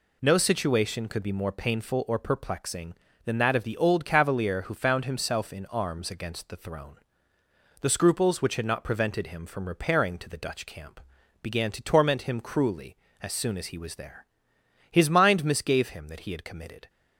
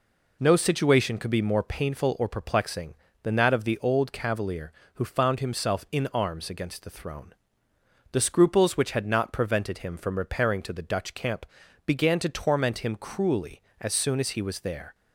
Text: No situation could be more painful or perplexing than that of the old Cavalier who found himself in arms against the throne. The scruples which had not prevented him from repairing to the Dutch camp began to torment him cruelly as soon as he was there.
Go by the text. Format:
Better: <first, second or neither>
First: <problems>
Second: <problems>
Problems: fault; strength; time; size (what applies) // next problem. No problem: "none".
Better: second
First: pauses between "camp" and "began"; at 10.9 s; 0.42 s long // goes on to say "His mind misgave him that he had committed"; strong; from 14.9 s on; 1.9 s long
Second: pauses between "camp" and "began"; at 11.4 s; 0.40 s long